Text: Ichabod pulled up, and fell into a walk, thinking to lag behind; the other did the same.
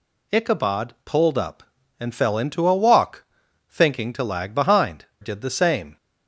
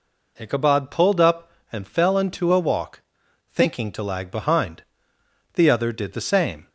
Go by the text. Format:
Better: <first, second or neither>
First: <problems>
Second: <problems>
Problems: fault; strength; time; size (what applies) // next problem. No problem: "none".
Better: second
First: skips "the other"; at 5.1 s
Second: none